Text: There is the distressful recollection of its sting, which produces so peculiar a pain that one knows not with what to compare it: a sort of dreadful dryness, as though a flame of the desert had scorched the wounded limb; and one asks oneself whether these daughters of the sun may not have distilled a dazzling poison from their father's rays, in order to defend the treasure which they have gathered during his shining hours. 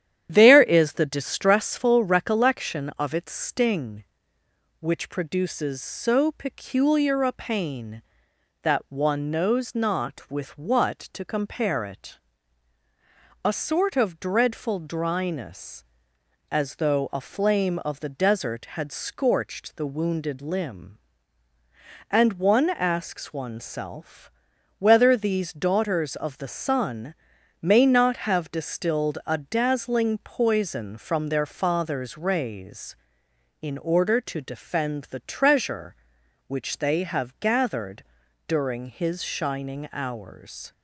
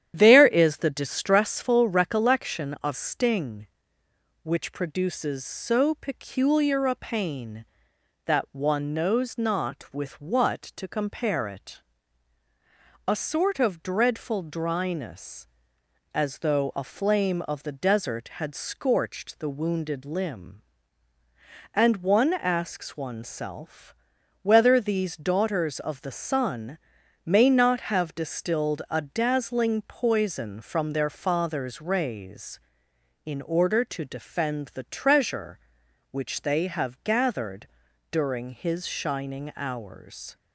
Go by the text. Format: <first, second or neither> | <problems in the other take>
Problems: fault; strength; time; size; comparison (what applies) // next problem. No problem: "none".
first | starts louder than the rest; strong; until 1.1 s; 10 dB; strong in the first // skips "its"; at 2.9 s // pauses between "oneself" and "whether"; noticeable; at 23.9 s; 0.48 s long; noticeable in the first // pauses between "sun" and "may"; noticeable; at 26.7 s; 0.46 s long; noticeable in the first // pauses between "gathered" and "during"; noticeable; at 37.6 s; 0.46 s long; noticeable in the first